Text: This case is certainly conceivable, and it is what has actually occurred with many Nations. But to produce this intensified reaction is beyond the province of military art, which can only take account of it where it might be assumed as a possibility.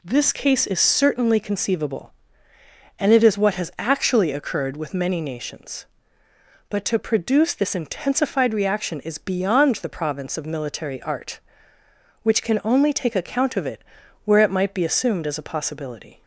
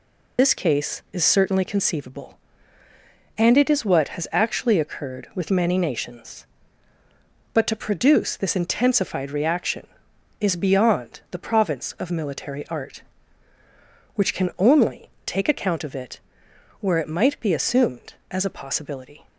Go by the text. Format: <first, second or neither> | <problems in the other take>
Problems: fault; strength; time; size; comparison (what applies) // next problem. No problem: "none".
first | loses the start of "This"; at 0.3 s; 45 ms // pauses between "only" and "take"; slight; at 15.1 s; 0.16 s long // pauses between "it" and "where"; noticeable; at 16.1 s; 0.62 s long; also in the first